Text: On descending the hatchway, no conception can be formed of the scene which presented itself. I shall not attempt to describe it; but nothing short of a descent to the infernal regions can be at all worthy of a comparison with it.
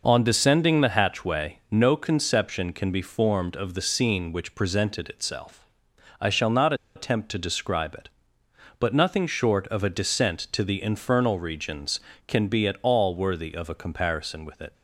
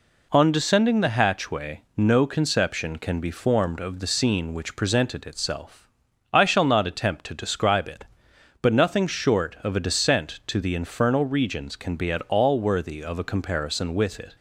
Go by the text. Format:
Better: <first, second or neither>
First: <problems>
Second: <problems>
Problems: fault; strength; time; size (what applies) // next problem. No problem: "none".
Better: second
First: pauses between "not" and "attempt"; slight; at 6.7 s; 0.21 s long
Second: none